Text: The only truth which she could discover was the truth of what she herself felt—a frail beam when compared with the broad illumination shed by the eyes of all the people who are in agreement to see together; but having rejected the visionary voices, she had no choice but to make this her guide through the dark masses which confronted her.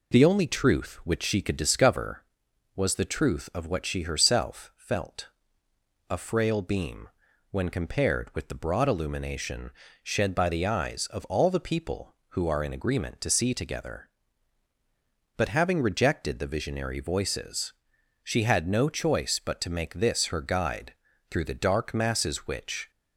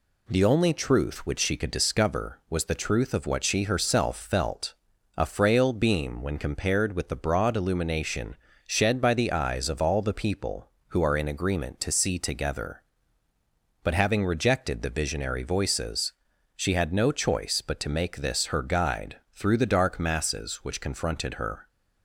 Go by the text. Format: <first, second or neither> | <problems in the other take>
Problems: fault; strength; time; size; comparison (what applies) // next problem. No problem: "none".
second | pauses between "beam" and "when"; at 7.0 s; 0.42 s long // pauses between "illumination" and "shed"; slight; at 9.7 s; 0.32 s long; slight in the second // pauses between "guide" and "through"; at 20.9 s; 0.38 s long // stops before "confronted her"; at 22.9 s